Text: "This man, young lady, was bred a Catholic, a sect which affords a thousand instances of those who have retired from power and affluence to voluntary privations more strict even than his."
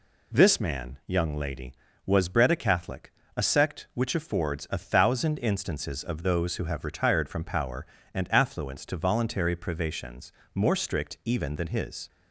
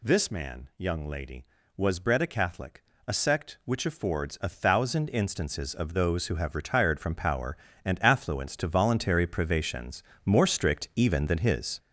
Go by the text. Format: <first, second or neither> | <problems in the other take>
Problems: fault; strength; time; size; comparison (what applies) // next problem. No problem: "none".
first | gets louder; throughout; 7 dB // pauses between "privations" and "more"; slight; at 10.0 s; 0.22 s long; slight in the first